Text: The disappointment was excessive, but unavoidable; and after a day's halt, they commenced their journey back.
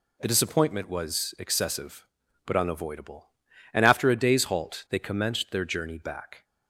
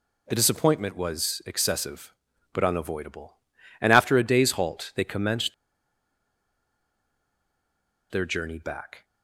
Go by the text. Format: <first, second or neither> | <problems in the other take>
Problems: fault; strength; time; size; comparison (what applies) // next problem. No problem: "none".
first | pauses between "commenced" and "their"; strong; at 5.5 s; 2.5 s long